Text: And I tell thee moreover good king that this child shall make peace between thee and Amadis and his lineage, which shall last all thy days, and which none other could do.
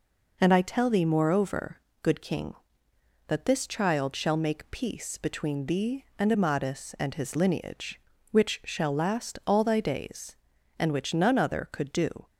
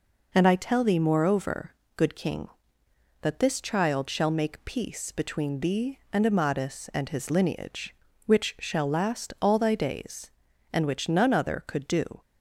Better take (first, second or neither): neither